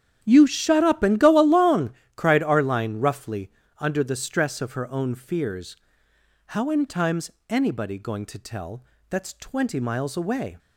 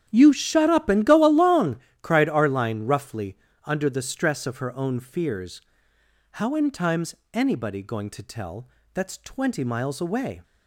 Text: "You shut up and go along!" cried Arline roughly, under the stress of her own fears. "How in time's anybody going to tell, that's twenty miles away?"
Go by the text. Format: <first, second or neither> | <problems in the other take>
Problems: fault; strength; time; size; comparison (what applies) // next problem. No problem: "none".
neither | starts louder than the rest; strong; the same in both // pauses between "time's" and "anybody"; slight; the same in both